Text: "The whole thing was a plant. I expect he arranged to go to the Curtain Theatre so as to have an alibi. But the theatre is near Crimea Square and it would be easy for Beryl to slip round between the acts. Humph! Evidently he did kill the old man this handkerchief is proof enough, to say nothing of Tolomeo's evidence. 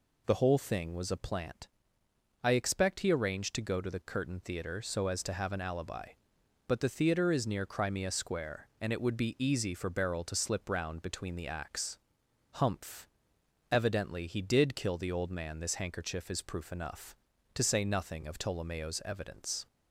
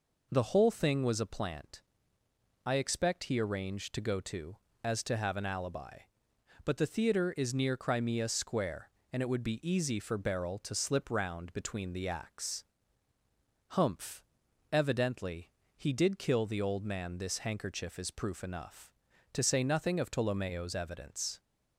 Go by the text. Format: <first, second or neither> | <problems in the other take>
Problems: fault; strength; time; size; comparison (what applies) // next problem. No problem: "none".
first | skips "the Curtain Theatre so"; at 4.7 s // pauses between "Evidently" and "he"; slight; at 15.5 s; 0.28 s long